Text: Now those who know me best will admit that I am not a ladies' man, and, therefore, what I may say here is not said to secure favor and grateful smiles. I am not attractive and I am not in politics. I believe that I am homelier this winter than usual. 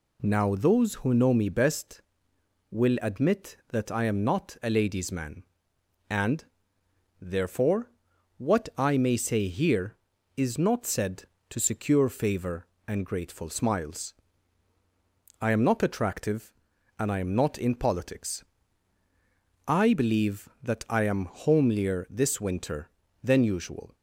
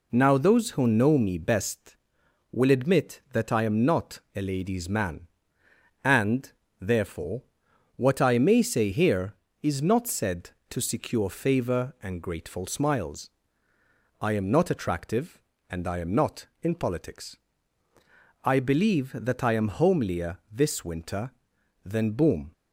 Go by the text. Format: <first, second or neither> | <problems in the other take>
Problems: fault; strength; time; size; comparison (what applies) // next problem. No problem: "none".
first | says "boom" for "usual"; at 22.1 s